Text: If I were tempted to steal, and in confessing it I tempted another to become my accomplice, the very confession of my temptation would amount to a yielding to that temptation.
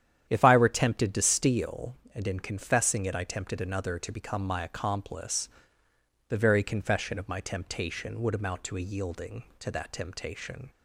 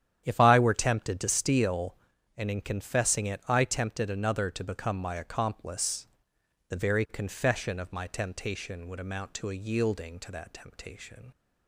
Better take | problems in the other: neither | starts louder than the rest; strong; the same in both

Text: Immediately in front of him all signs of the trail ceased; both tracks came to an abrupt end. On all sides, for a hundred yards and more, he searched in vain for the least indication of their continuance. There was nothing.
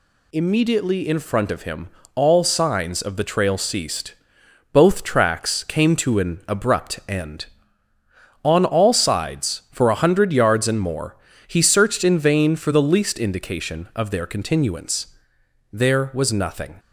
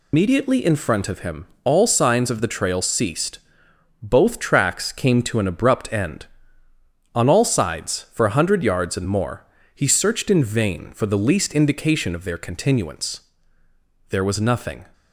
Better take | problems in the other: first | loses the start of "Immediately"; at 0.1 s; 140 ms // pauses between "him" and "all"; slight; at 1.4 s; 0.16 s long; slight in the first

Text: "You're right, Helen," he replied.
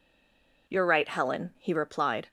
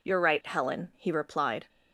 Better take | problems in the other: second | stays silent before the first word; slight; until 0.6 s; 0.6 s long

